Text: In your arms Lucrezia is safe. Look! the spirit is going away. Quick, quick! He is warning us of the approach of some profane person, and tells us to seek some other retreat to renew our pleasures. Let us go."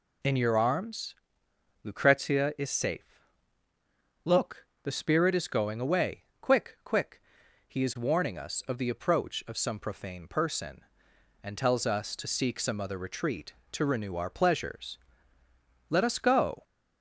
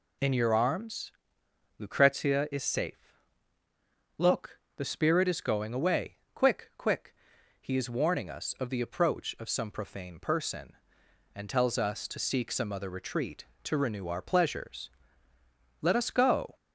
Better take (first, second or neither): neither